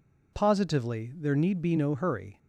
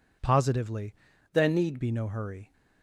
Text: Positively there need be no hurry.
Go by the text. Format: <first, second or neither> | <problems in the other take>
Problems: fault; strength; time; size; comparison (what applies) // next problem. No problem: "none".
first | changes voice from "there" to "need"; from 1.3 to 1.8 s; 0.5 s long